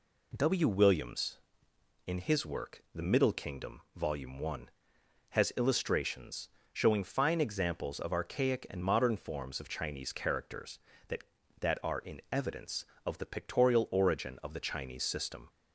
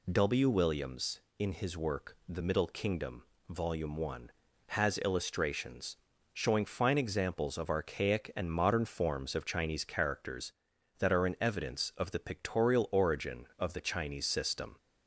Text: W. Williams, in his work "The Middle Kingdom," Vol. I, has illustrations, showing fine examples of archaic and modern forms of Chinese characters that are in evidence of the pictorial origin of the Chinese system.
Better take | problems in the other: second | says "that" twice; at 11.5 s

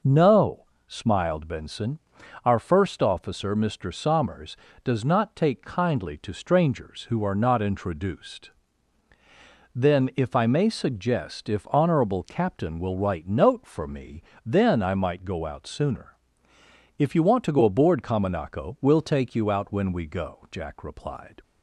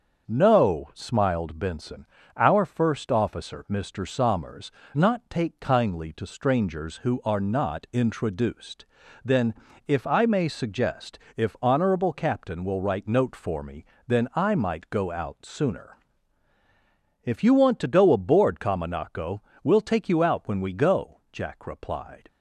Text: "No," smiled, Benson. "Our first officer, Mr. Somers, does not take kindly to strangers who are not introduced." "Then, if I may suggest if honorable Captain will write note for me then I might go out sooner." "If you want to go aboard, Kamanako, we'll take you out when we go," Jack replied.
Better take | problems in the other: first | starts louder than the rest; until 1.3 s; 6.5 dB // skips "does"; at 4.8 s // pauses between "suggest" and "if"; slight; at 11.1 s; 0.18 s long // pauses between "me" and "then"; slight; at 13.8 s; 0.20 s long; slight in the first

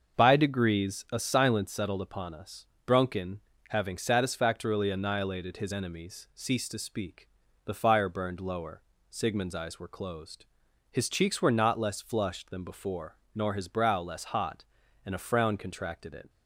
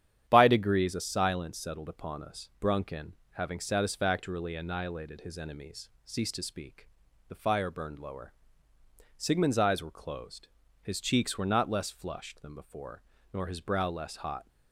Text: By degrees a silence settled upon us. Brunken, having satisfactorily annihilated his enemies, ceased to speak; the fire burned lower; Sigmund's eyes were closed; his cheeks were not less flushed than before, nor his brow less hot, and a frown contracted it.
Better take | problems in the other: first | starts louder than the rest; strong; until 1.3 s; 9.5 dB; also in the first // stops before "and a frown contracted it"; at 14.4 s

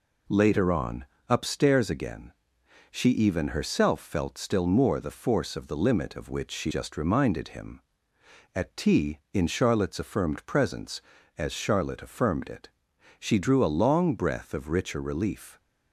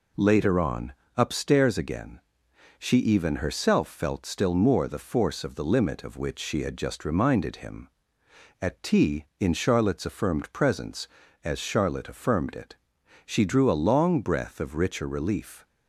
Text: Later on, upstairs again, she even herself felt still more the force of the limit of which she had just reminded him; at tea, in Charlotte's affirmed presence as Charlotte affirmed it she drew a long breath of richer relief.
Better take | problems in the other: second | skips "had"; at 6.7 s // pauses between "it" and "she"; noticeable; at 12.6 s; 0.50 s long; noticeable in the second

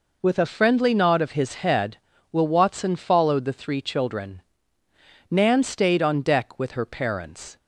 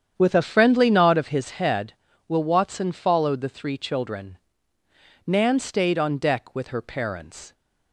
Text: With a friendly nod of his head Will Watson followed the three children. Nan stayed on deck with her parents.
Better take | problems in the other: first | starts louder than the rest; strong; until 1.4 s; 8.5 dB

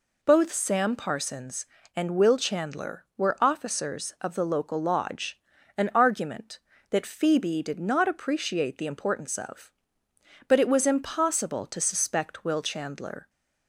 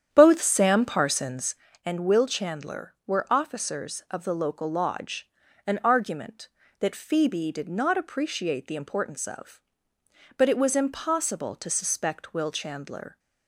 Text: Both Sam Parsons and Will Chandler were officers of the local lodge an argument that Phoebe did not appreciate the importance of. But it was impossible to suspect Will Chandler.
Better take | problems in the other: first | starts louder than the rest; strong; until 1.6 s; 9 dB // pauses between "lodge" and "an"; at 5.2 s; 0.38 s long; also in the first

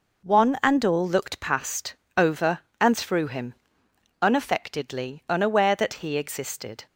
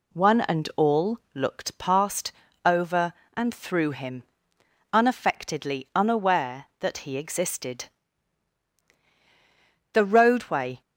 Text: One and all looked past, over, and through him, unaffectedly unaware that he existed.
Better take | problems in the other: first | pauses between "all" and "looked"; slight; at 1.1 s; 0.16 s long // goes on to say "The roadway"; noticeable; from 9.9 s on; 0.88 s long

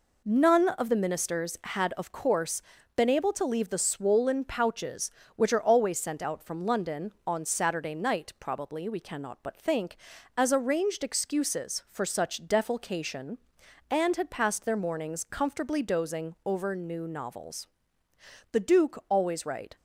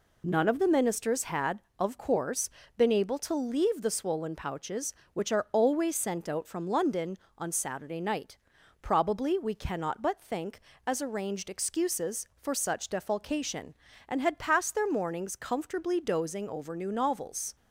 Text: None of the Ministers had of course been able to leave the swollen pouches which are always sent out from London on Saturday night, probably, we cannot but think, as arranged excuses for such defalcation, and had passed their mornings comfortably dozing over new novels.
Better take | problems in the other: second | pauses between "course" and "been"; slight; at 2.6 s; 0.34 s long; slight in the second // goes on to say "The Duke always right"; noticeable; from 18.5 s on; 1.2 s long

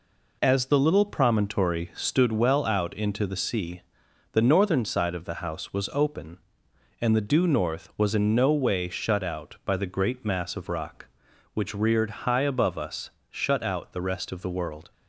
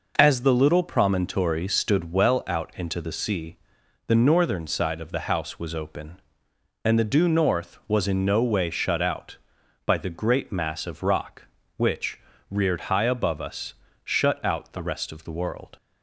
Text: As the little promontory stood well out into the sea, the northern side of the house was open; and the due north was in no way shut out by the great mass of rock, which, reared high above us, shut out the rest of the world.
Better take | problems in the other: neither | none

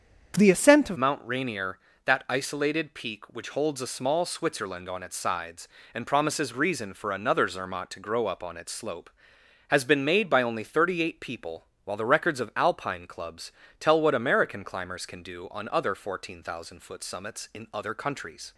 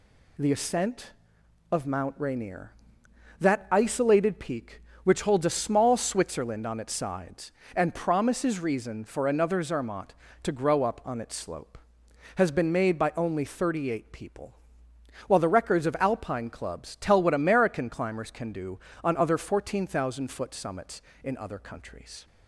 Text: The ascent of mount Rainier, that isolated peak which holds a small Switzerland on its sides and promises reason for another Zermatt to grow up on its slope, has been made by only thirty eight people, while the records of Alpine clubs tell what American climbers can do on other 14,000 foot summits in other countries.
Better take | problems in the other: second | starts louder than the rest; strong; until 1.4 s; 7.5 dB // changes voice at "mount"; from 0.9 s on; 17.6 s long // pauses between "clubs" and "tell"; slight; at 13.4 s; 0.30 s long

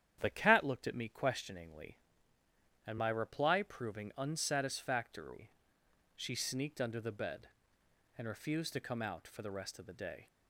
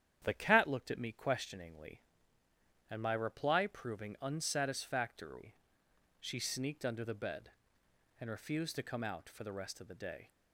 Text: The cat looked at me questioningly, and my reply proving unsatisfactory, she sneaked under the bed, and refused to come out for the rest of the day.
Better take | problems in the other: neither | starts louder than the rest; strong; the same in both

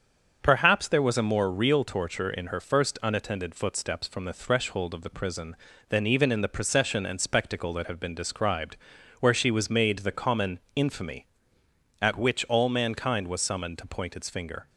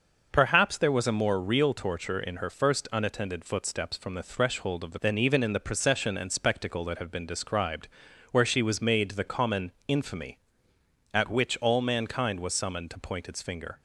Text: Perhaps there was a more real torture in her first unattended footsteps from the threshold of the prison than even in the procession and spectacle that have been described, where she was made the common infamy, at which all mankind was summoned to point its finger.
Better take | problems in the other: first | starts louder than the rest; noticeable; until 1.3 s; 6 dB; also in the first // skips "prison"; at 5.0 s // pauses between "common" and "infamy"; slight; at 9.7 s; 0.18 s long; slight in the first

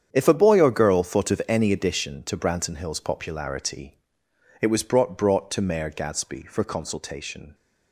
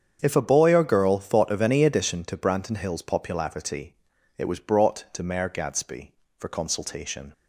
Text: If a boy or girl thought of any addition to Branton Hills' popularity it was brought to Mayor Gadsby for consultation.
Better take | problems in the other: second | starts louder than the rest; strong; until 1.1 s; 8.5 dB; strong in the second // pauses between "popularity" and "it"; noticeable; at 3.9 s; 0.64 s long; also in the second // says "brought" twice; at 5.1 s

